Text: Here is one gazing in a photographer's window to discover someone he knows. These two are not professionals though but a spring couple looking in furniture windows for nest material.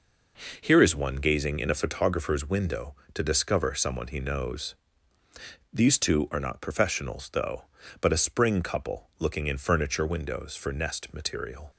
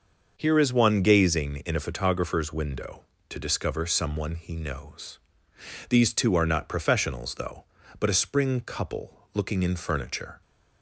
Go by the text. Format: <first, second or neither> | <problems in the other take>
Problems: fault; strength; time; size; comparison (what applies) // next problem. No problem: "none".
first | starts louder than the rest; until 1.3 s; 6.5 dB // pauses between "couple" and "looking"; slight; at 9.1 s; 0.18 s long // stops before "windows for nest material"; at 10.4 s